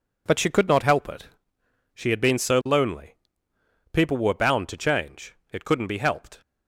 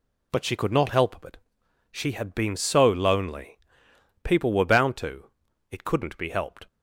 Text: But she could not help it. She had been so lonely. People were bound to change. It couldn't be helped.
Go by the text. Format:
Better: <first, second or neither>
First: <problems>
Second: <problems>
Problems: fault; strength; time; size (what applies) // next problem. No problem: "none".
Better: first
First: none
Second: skips "change"; at 5.4 s